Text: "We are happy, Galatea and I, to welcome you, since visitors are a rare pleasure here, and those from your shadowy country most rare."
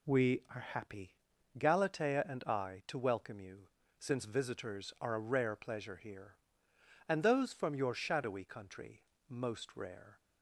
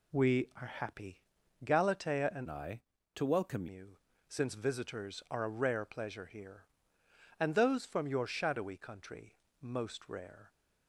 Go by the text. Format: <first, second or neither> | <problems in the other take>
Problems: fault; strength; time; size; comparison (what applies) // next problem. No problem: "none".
first | changes voice from "I" to "welcome"; from 2.4 to 3.6 s; 1.2 s long // pauses between "country" and "most"; slight; at 9.3 s; 0.26 s long; slight in the first